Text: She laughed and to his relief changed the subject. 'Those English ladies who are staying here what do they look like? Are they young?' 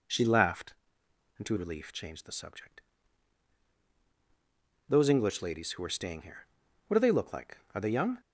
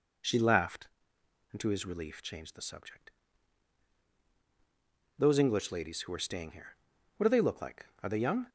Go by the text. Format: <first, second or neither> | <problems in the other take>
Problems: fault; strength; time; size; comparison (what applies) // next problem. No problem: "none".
second | skips "his"; at 1.5 s // pauses between "here" and "what"; at 6.4 s; 0.42 s long; also in the second